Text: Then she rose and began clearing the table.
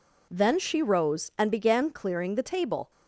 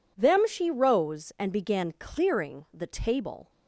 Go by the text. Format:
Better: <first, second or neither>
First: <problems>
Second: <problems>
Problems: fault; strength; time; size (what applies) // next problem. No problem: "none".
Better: first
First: none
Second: says "Them" for "Then"; at 0.1 s